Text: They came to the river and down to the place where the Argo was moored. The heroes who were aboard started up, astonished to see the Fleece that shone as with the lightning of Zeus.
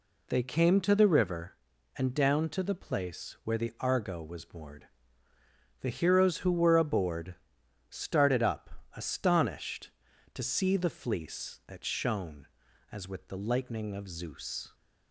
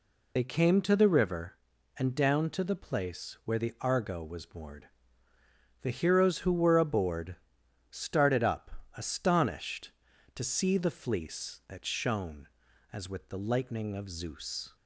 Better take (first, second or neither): first